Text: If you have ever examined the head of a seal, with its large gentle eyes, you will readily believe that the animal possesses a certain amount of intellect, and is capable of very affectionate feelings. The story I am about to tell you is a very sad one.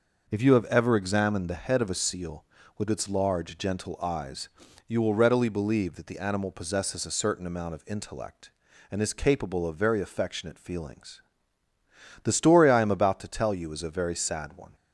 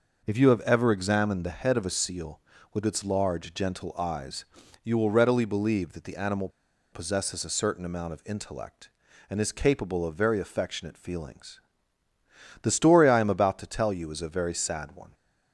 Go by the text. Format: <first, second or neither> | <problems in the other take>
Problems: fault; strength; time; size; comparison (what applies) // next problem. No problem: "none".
first | pauses between "animal" and "possesses"; at 6.4 s; 0.44 s long